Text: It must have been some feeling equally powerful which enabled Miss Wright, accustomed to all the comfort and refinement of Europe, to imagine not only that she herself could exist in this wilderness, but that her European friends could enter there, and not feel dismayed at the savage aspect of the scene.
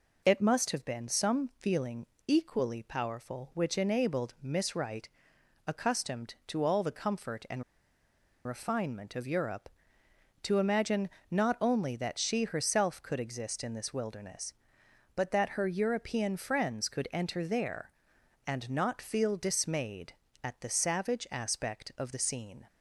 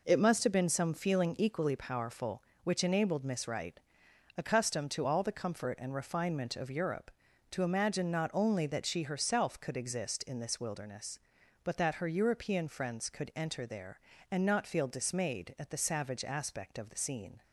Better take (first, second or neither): second